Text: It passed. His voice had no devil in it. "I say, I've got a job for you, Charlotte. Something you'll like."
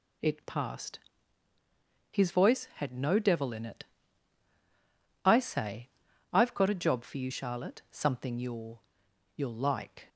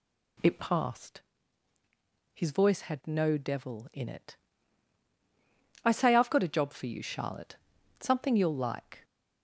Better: second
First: says "you'll" twice; at 9.3 s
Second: none

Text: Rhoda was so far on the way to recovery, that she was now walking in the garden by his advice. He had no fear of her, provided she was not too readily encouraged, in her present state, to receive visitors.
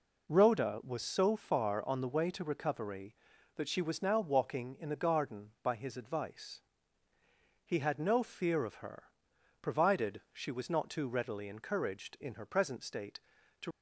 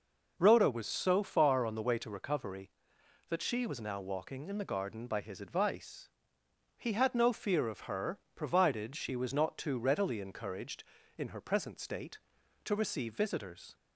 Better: second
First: stops before "receive visitors"; at 13.7 s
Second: none

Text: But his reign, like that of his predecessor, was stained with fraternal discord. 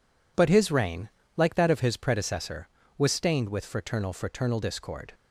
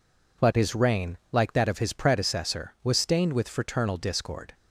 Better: second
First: says "fraternal" twice; at 4.1 s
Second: none

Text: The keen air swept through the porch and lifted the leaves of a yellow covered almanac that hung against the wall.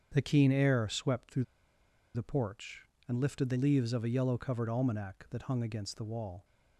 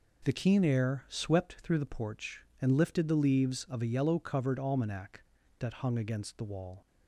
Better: second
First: starts louder than the rest; strong; until 1.1 s; 7.5 dB // pauses between "through" and "the"; noticeable; at 1.4 s; 0.70 s long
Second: none

